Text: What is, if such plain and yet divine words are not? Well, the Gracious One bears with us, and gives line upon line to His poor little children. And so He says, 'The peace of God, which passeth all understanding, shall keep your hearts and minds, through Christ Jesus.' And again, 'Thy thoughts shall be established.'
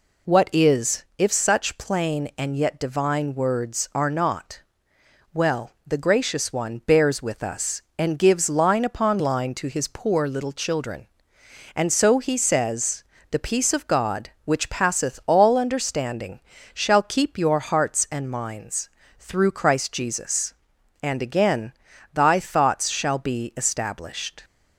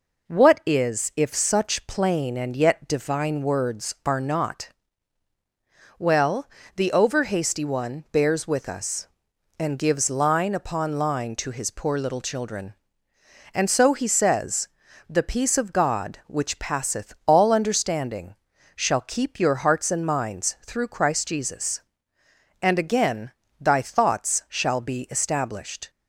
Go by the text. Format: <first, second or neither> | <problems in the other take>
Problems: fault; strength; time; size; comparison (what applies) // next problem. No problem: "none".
first | says "Overhasty" for "Gracious"; at 6.9 s